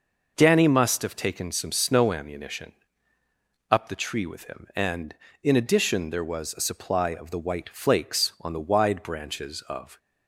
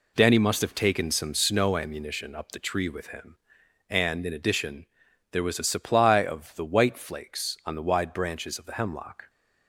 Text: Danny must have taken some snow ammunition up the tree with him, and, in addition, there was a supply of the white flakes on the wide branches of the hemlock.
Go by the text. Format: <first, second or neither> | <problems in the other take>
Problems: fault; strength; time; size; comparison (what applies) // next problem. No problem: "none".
second | pauses between "ammunition" and "up"; noticeable; at 2.7 s; 0.98 s long // stops before "the hemlock"; at 9.9 s